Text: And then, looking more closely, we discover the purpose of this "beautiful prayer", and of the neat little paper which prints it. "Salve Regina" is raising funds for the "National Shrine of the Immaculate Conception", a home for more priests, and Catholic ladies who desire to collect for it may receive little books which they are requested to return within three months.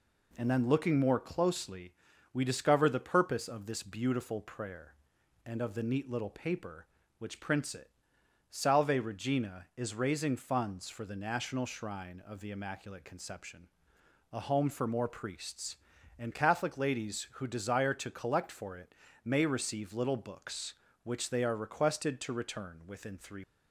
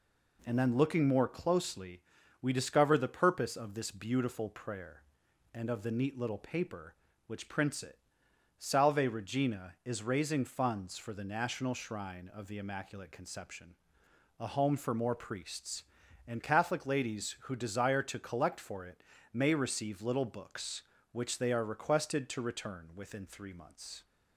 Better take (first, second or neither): second